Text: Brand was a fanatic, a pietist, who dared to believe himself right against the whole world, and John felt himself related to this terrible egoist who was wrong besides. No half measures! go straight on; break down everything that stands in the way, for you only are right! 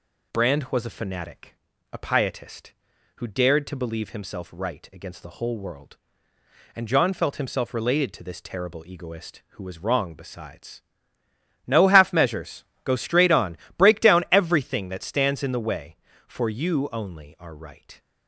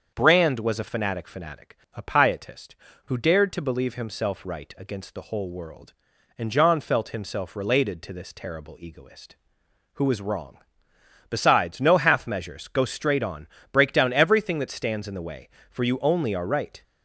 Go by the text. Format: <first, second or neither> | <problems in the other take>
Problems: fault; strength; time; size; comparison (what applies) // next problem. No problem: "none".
first | starts louder than the rest; until 1.1 s; 7 dB // says "fanatic" twice; at 1.2 s // pauses between "wrong" and "besides"; noticeable; at 10.5 s; 0.70 s long